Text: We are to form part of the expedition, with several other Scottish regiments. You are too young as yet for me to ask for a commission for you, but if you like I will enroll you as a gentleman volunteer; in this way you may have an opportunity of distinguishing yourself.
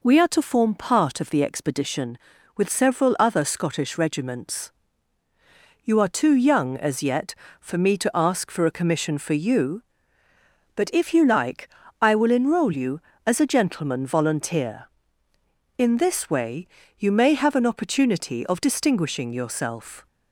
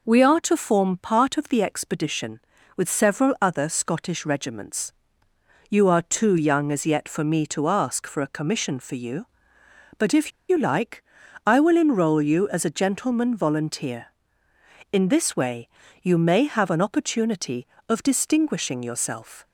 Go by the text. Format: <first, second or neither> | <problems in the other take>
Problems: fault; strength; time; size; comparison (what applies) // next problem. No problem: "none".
first | pauses between "if" and "you"; slight; at 10.3 s; 0.18 s long // pauses between "like" and "I"; at 11.0 s; 0.42 s long; slight in the first // pauses between "way" and "you"; slight; at 15.6 s; 0.36 s long; slight in the first